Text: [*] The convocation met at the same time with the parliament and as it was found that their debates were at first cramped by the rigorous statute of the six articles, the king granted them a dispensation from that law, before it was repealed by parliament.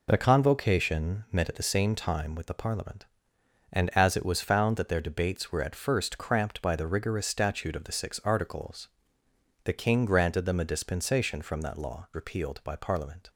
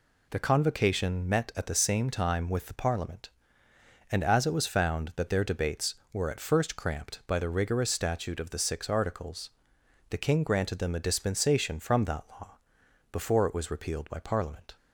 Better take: second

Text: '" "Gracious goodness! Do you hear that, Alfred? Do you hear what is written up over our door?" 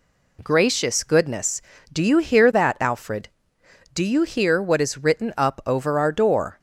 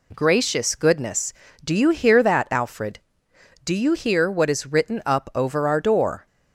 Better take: neither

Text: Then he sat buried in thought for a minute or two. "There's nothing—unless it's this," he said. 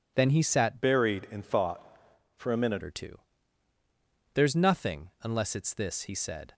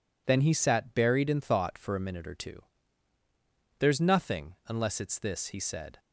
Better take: second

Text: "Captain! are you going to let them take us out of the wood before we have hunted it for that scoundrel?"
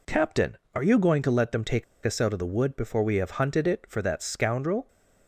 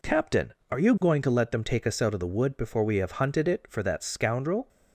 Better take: second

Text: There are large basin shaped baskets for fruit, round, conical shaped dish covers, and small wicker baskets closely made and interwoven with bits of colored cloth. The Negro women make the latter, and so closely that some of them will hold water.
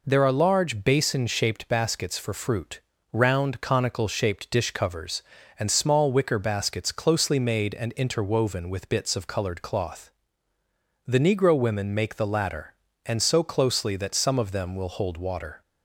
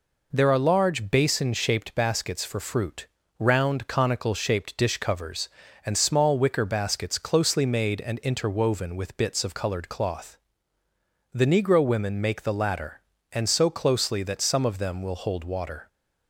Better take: neither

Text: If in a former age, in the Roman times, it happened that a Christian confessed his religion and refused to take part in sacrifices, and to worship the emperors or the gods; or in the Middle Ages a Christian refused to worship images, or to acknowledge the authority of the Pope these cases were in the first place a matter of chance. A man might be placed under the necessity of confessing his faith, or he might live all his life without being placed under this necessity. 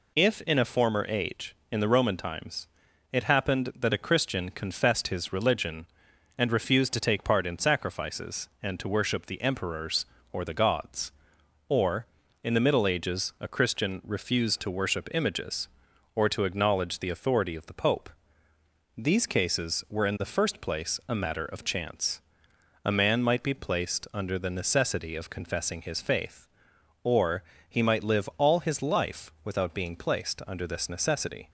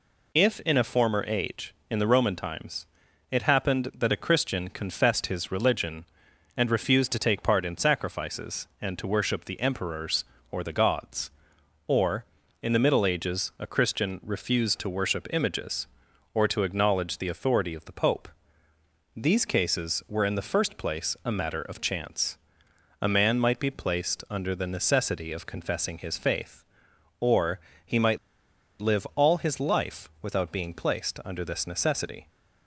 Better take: first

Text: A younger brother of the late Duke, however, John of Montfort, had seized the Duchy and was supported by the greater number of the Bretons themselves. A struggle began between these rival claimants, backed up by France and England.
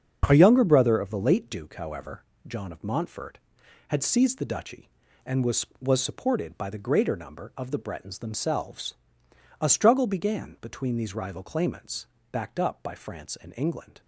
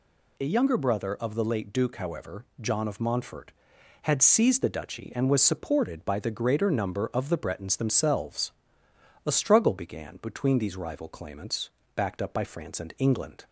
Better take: second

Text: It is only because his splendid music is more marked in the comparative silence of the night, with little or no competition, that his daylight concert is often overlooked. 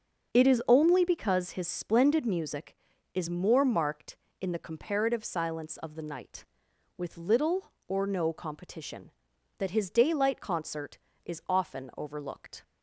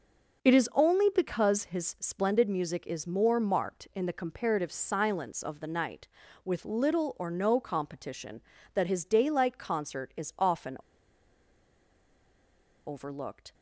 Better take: first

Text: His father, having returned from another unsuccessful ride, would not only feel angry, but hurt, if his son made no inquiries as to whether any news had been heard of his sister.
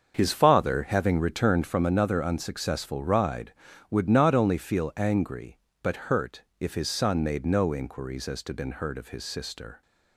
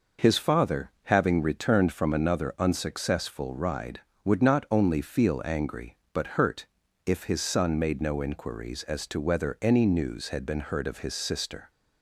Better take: second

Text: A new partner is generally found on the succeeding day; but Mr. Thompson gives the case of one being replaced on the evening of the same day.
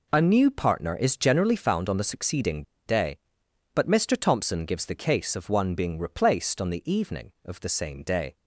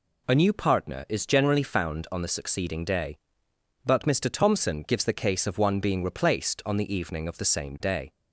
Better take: second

